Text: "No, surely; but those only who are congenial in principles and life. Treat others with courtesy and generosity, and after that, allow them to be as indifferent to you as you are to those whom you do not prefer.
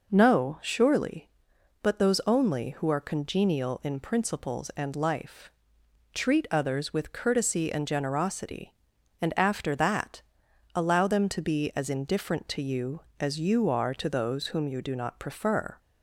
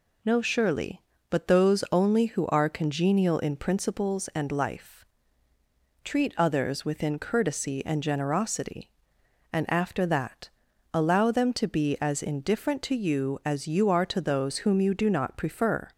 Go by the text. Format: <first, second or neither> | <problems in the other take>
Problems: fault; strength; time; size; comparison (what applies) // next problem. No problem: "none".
first | says "within" for "with"; at 6.8 s